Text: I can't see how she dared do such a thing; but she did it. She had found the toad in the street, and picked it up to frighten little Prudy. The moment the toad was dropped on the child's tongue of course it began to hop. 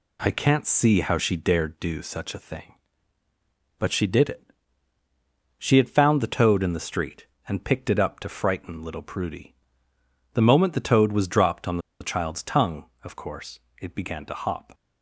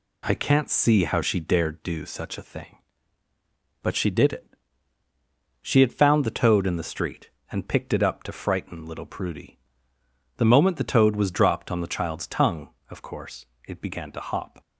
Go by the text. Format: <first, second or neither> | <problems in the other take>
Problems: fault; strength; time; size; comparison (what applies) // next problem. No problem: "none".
second | pauses between "on" and "the"; slight; at 11.7 s; 0.21 s long // pauses between "course" and "it"; slight; at 13.5 s; 0.22 s long; slight in the second